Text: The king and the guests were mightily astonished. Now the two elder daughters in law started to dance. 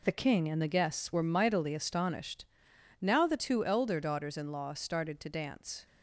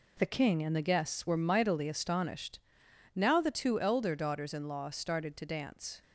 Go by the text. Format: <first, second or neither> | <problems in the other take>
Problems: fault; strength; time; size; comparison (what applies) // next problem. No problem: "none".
neither | none